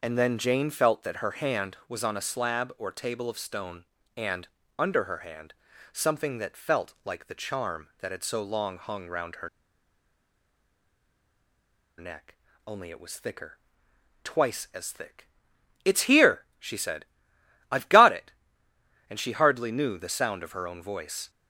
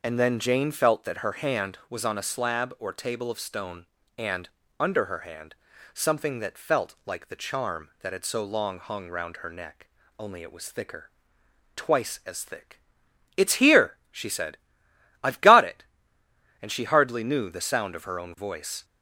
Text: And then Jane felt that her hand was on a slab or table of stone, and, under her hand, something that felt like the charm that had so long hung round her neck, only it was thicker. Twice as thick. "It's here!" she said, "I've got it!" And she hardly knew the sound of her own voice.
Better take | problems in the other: second | pauses between "her" and "neck"; strong; at 9.4 s; 2.4 s long

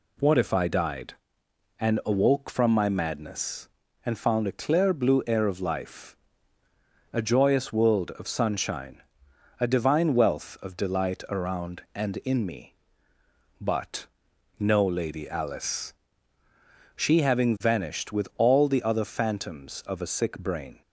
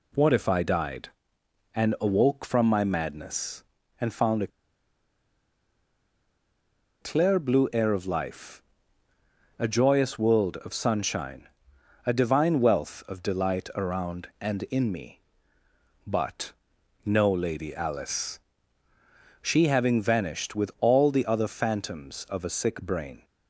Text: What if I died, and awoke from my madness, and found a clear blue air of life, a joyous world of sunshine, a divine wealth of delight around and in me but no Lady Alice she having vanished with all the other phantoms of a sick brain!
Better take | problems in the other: first | pauses between "a" and "clear"; strong; at 4.5 s; 2.5 s long // pauses between "but" and "no"; noticeable; at 16.5 s; 0.54 s long; noticeable in the first // pauses between "Alice" and "she"; at 18.3 s; 1.0 s long; also in the first

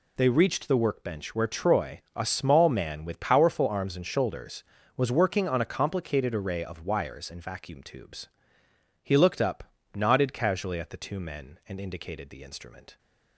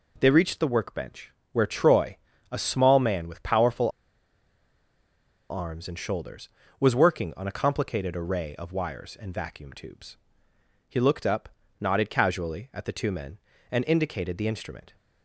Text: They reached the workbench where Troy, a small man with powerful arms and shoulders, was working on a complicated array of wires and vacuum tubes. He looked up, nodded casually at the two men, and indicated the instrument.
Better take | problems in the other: first | pauses between "workbench" and "where"; slight; at 1.3 s; 0.22 s long // pauses between "powerful" and "arms"; strong; at 3.9 s; 1.5 s long

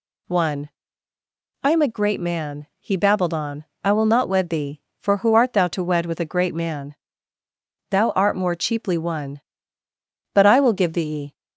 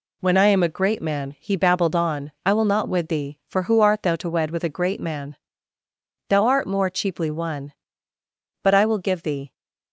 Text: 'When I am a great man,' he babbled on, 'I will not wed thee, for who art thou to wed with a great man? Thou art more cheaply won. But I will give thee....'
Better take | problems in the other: second | says "One" for "When"; at 0.2 s

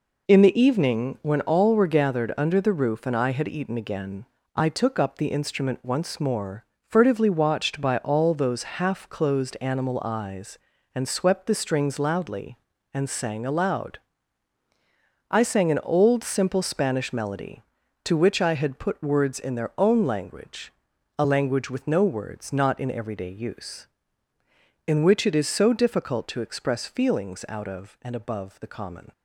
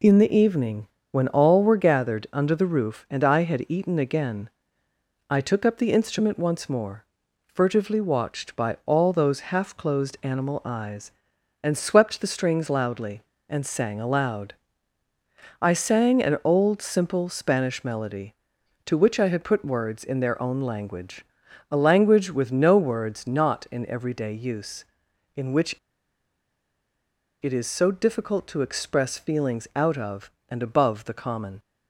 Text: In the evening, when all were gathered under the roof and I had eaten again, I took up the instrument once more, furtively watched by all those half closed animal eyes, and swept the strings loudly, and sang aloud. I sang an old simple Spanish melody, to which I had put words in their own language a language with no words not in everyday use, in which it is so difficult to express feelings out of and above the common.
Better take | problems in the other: first | pauses between "language" and "a"; noticeable; at 21.2 s; 0.46 s long; noticeable in the first // pauses between "which" and "it"; strong; at 25.7 s; 1.6 s long

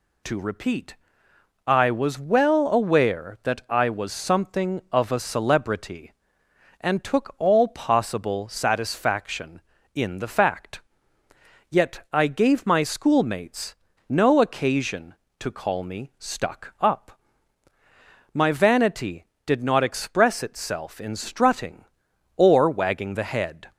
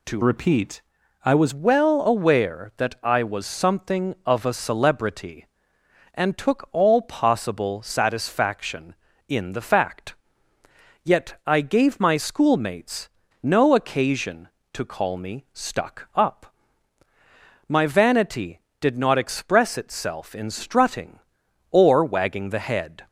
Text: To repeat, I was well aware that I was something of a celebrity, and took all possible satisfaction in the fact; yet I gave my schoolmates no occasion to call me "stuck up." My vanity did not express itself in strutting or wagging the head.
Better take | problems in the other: first | changes voice from "repeat" to "was"; from 0.2 to 1.5 s; 1.3 s long // pauses between "schoolmates" and "no"; slight; at 13.0 s; 0.32 s long; slight in the first

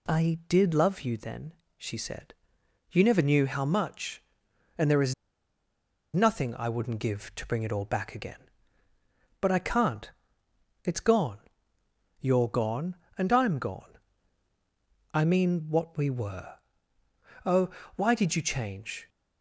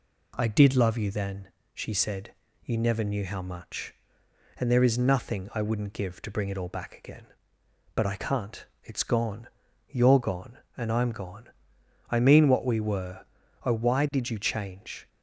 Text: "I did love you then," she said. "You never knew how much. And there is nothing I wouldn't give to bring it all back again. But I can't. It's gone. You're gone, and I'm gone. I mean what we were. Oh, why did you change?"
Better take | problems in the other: second | pauses between "is" and "nothing"; at 5.1 s; 1.0 s long

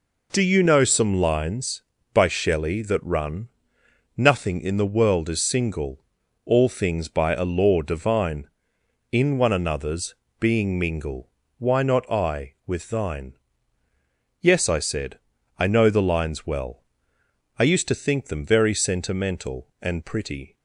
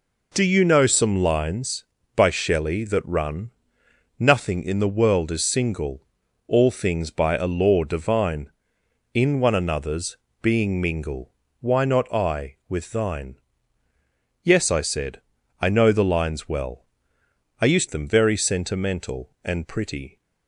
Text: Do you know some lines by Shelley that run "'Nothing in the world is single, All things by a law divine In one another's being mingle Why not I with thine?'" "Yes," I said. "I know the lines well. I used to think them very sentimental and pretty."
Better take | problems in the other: first | pauses between "run" and "Nothing"; noticeable; at 3.5 s; 0.68 s long; noticeable in the first // pauses between "another's" and "being"; slight; at 10.1 s; 0.24 s long; slight in the first // pauses between "mingle" and "Why"; slight; at 11.3 s; 0.28 s long; slight in the first // skips "to think"; at 17.8 s

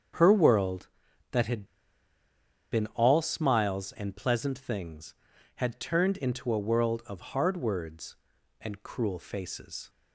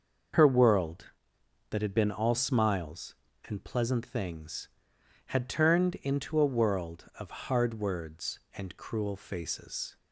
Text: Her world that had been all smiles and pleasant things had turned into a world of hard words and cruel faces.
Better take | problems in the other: second | starts louder than the rest; strong; until 1.6 s; 7.5 dB; noticeable in the second // pauses between "had" and "been"; at 1.6 s; 1.0 s long

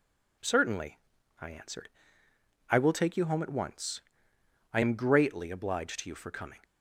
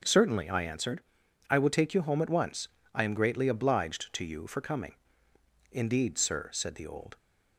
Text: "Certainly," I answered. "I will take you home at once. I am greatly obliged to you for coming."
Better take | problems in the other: first | starts louder than the rest; noticeable; until 1.5 s; 6 dB // goes on to say "Indeed sir said the old"; from 5.7 s on; 1.4 s long

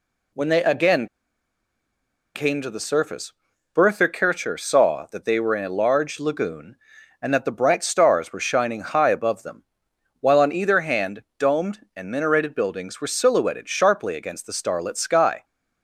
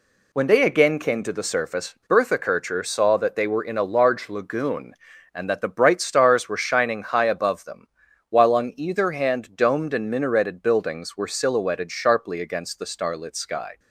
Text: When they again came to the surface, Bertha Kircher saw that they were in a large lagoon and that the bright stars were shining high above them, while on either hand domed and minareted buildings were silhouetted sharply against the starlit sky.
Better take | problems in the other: second | pauses between "again" and "came"; strong; at 1.0 s; 1.2 s long

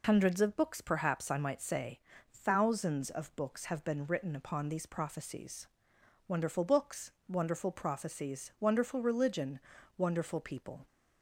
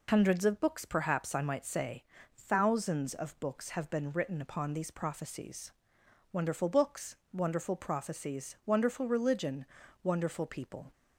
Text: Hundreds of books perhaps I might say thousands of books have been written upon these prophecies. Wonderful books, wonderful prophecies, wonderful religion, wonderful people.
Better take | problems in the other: neither | pauses between "say" and "thousands"; slight; the same in both

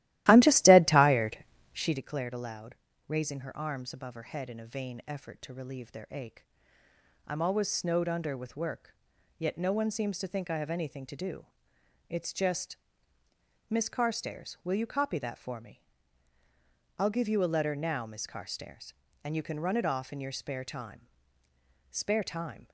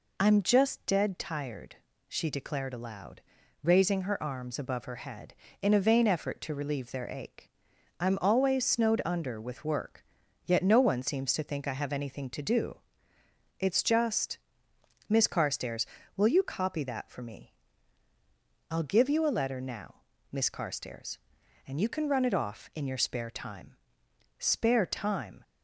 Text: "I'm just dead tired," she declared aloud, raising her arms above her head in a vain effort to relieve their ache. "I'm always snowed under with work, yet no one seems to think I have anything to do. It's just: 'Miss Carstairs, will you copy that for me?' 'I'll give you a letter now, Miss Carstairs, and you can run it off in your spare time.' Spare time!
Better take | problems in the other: second | starts louder than the rest; strong; until 2.0 s; 15.5 dB

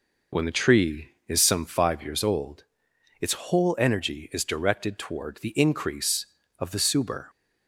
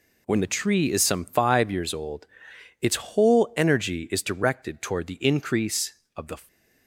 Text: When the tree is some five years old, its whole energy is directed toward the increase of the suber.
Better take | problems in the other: first | stops before "suber"; at 6.4 s

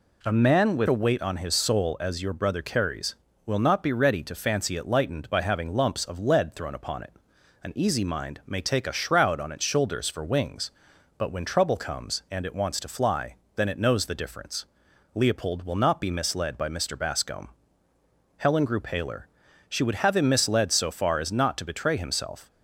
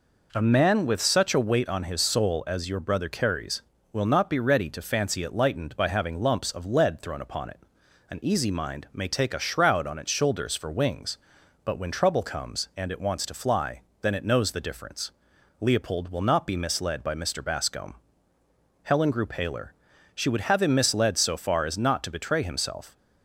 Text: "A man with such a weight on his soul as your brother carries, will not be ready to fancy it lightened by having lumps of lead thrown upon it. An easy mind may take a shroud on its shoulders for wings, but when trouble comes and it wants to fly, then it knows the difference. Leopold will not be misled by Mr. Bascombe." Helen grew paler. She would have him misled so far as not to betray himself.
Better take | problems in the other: second | skips "such"; at 0.8 s

